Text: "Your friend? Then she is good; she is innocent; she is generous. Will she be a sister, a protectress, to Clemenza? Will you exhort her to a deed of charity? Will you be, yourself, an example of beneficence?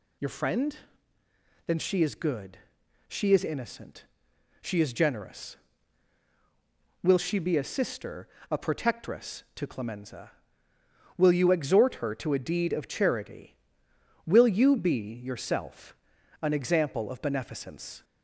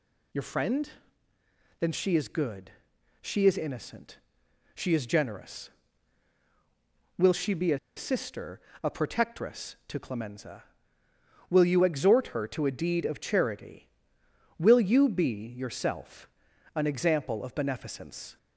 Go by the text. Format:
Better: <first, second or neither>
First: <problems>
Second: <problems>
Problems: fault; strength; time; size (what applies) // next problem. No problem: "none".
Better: first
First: none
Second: pauses between "a" and "sister"; slight; at 7.7 s; 0.18 s long